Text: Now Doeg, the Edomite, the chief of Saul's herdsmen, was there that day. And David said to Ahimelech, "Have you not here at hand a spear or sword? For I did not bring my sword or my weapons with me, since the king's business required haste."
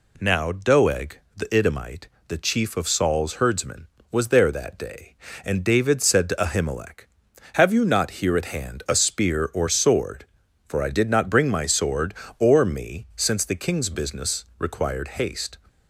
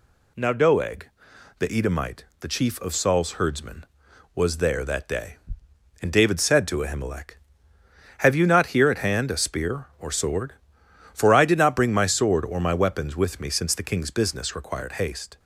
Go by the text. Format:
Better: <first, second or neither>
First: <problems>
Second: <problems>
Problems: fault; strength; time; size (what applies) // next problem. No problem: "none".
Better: second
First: skips "my weapons with"; at 12.6 s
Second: none